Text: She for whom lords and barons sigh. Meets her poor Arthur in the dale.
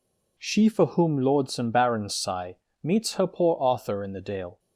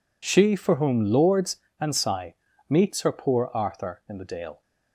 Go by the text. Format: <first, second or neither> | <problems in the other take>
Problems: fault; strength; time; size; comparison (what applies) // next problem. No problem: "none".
first | skips "barons"; at 1.9 s